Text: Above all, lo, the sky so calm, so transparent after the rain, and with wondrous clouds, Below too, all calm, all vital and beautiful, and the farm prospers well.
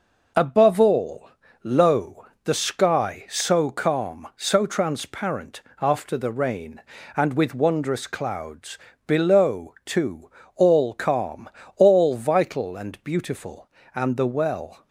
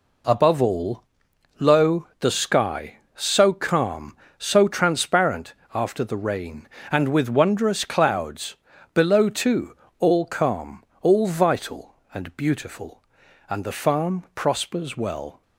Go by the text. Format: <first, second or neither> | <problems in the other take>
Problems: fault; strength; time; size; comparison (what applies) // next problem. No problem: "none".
second | pauses between "transparent" and "after"; slight; at 5.5 s; 0.22 s long; slight in the second // skips "farm prospers"; at 14.2 s